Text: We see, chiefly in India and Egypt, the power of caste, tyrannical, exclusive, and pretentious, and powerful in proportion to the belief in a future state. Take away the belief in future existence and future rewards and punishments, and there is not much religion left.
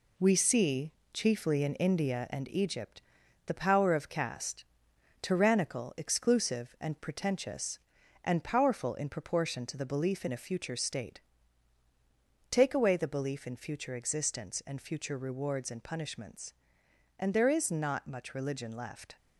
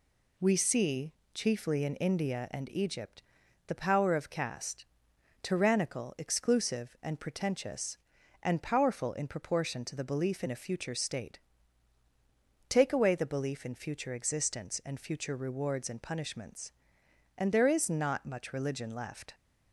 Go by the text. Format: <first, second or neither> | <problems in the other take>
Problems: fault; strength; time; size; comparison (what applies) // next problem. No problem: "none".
second | gets quieter; noticeable; throughout; 5.5 dB